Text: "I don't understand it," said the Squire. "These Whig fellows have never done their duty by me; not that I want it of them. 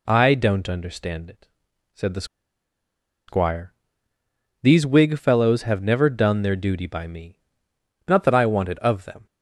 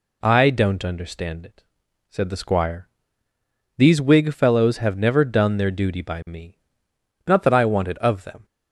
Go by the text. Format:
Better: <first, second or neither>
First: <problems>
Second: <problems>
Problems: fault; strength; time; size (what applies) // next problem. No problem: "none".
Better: second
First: pauses between "the" and "Squire"; at 2.2 s; 1.0 s long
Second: none